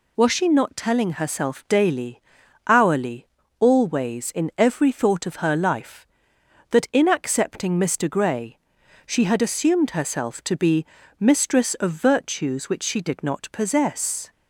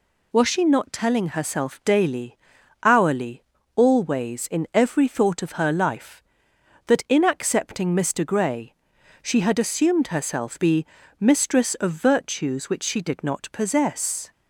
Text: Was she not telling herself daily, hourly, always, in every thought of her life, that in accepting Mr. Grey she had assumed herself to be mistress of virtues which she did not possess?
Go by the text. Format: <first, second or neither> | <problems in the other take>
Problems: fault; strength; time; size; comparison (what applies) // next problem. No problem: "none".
first | pauses between "Grey" and "she"; noticeable; at 8.7 s; 0.50 s long; noticeable in the first // skips "to"; at 10.5 s // pauses between "be" and "mistress"; slight; at 10.8 s; 0.36 s long; slight in the first